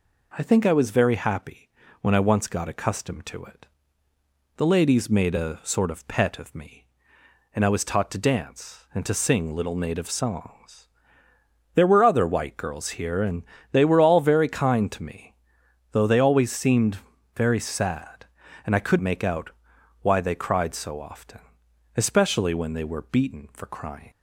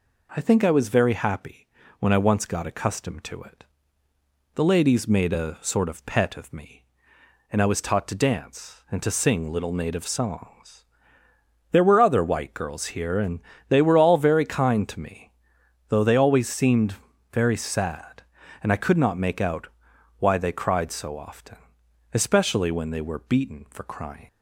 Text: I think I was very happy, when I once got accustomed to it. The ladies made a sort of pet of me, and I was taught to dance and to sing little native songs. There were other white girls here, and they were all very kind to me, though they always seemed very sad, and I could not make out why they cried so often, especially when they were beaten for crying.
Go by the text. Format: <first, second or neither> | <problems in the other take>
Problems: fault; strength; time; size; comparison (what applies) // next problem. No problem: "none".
second | pauses between "and" and "they"; slight; at 13.4 s; 0.30 s long; slight in the second // pauses between "seemed" and "very"; at 16.9 s; 0.40 s long; also in the second // skips "not"; at 18.9 s // pauses between "out" and "why"; noticeable; at 19.4 s; 0.52 s long; noticeable in the second